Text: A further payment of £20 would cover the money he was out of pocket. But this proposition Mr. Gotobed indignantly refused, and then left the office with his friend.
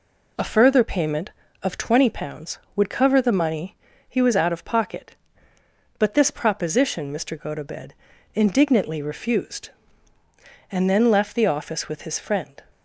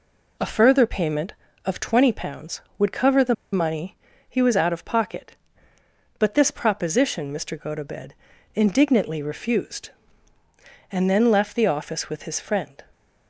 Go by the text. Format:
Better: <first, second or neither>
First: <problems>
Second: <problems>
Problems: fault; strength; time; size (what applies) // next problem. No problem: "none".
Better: first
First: pauses between "money" and "he"; slight; at 3.7 s; 0.34 s long // pauses between "Gotobed" and "indignantly"; at 7.9 s; 0.40 s long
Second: pauses between "the" and "money"; slight; at 3.3 s; 0.18 s long // pauses between "money" and "he"; slight; at 3.9 s; 0.34 s long // pauses between "Gotobed" and "indignantly"; at 8.1 s; 0.40 s long